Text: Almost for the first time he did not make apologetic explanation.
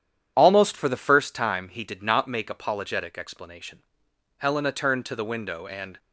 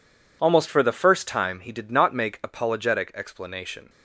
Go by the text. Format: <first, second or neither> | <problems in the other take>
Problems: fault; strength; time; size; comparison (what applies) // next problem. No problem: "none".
second | starts louder than the rest; strong; until 1.3 s; 9.5 dB // goes on to say "Helena turned to the window and"; from 4.3 s on; 1.6 s long